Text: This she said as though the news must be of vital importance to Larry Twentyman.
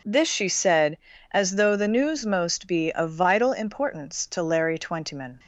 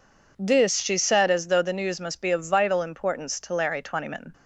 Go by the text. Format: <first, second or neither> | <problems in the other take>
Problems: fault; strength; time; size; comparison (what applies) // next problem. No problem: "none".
second | says "most" for "must"; at 2.2 s